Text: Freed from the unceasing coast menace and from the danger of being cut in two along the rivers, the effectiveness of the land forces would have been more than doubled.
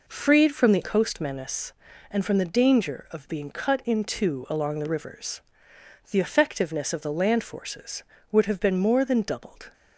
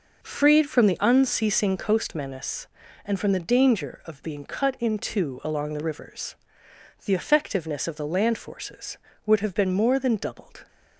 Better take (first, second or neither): second